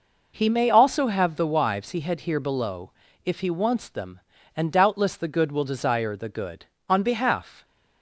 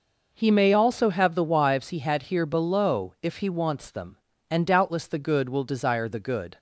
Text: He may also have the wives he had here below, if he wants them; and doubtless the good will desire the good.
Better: second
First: goes on to say "On behalf"; noticeable; from 6.8 s on; 0.76 s long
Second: none

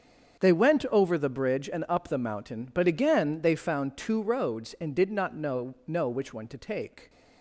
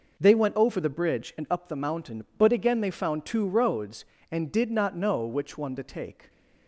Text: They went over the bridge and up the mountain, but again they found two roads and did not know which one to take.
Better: second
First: starts louder than the rest; until 1.4 s; 6.5 dB // says "know" twice; at 5.8 s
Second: none

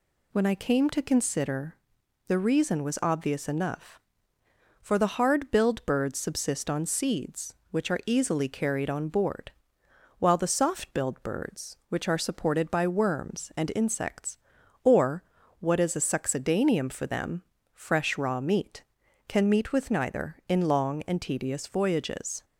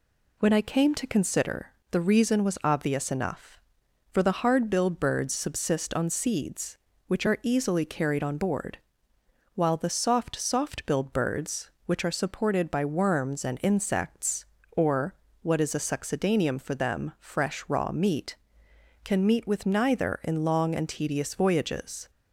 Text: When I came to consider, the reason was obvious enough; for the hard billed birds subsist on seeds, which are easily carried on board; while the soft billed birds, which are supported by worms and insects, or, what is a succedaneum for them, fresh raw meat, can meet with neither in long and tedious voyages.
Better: first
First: none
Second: says "soft" twice; at 10.3 s

